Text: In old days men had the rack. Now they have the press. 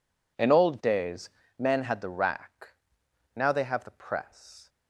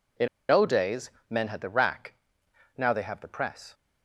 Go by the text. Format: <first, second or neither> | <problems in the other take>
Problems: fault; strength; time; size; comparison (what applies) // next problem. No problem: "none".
first | pauses between "In" and "old"; slight; at 0.2 s; 0.23 s long // pauses between "days" and "men"; slight; at 1.0 s; 0.20 s long; slight in the first